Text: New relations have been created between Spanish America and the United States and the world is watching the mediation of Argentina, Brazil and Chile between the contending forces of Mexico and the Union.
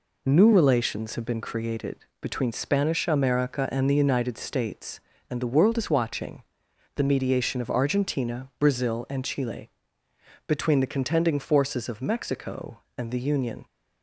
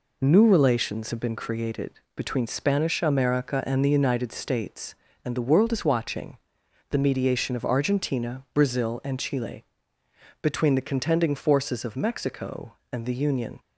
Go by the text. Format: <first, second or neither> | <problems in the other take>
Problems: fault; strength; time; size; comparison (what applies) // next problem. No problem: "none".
neither | pauses between "created" and "between"; slight; the same in both // pauses between "watching" and "the"; noticeable; the same in both // pauses between "Chile" and "between"; noticeable; the same in both